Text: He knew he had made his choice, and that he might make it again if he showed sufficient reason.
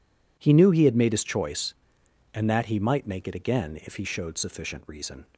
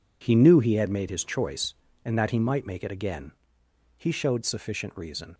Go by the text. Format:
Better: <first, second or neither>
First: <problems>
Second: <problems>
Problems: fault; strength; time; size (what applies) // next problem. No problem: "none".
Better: first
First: none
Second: skips "if"; at 3.6 s